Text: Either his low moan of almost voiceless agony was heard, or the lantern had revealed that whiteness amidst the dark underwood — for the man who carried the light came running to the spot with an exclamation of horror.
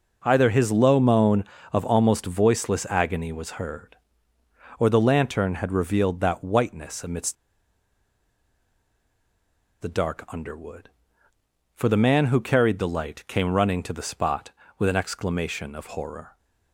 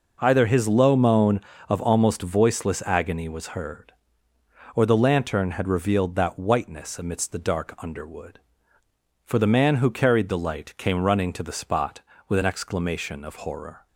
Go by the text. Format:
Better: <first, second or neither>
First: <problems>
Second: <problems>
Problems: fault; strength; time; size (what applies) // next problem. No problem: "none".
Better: second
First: pauses between "amidst" and "the"; strong; at 7.3 s; 2.4 s long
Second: none